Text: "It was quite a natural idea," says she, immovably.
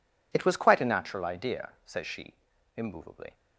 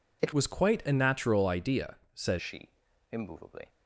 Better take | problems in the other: first | changes voice from "was" to "says"; from 0.3 to 2.3 s; 2.0 s long

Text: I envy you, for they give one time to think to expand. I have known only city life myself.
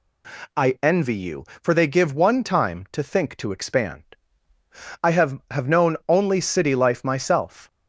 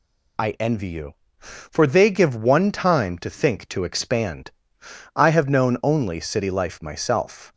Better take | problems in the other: second | says "have" twice; at 5.5 s

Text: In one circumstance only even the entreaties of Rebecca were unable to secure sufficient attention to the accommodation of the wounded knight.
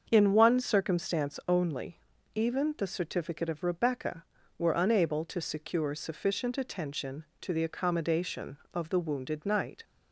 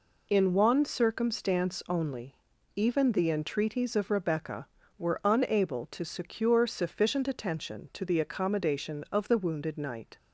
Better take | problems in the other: second | starts louder than the rest; until 1.1 s; 6.5 dB // pauses between "only" and "even"; slight; at 1.9 s; 0.34 s long; also in the second // says "certificate" for "entreaties"; at 2.8 s

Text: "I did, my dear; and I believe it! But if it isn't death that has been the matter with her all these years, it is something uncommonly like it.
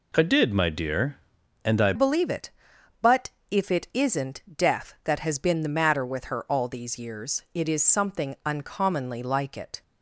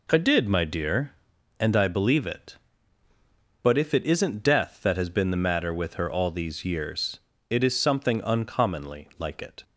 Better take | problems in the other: second | changes voice at "believe"; from 1.9 s on; 7.9 s long // pauses between "But" and "if"; slight; at 3.3 s; 0.22 s long

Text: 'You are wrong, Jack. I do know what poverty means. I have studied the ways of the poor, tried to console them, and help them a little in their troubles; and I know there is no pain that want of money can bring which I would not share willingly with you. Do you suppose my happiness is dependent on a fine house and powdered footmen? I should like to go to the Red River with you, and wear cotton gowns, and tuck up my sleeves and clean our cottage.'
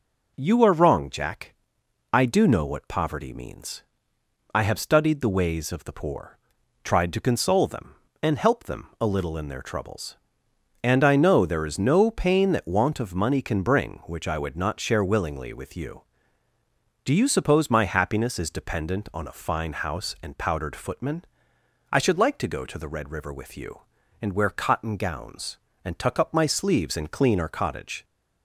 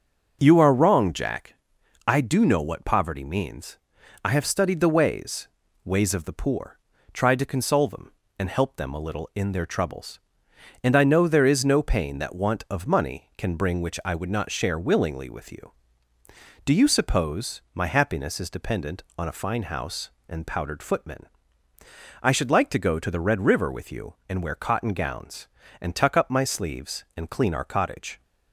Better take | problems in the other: first | starts louder than the rest; noticeable; until 1.4 s; 6 dB // says "ways" twice; at 5.8 s

